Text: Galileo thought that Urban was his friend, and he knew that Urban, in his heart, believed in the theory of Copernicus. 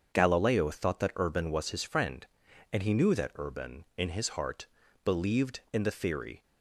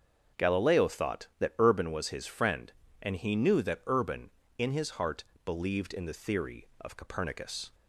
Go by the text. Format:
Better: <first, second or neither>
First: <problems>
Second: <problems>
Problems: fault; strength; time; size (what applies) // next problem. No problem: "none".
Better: second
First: starts louder than the rest; until 1.1 s; 7 dB // stops before "of Copernicus"; at 6.4 s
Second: starts louder than the rest; until 1.4 s; 7 dB